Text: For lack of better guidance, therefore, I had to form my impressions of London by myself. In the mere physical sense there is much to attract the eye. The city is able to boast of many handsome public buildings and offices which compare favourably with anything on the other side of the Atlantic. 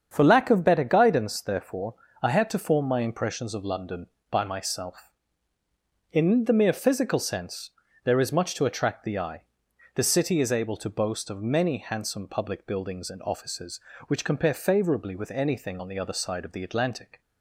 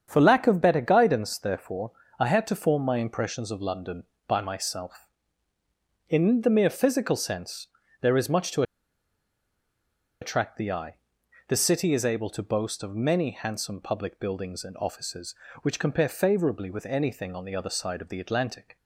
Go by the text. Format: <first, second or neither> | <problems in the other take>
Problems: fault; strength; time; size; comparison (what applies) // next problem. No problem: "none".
first | starts louder than the rest; strong; until 1.0 s; 7.5 dB; strong in the first // pauses between "sense" and "there"; slight; at 7.6 s; 0.34 s long; slight in the first // pauses between "to" and "attract"; strong; at 8.6 s; 1.5 s long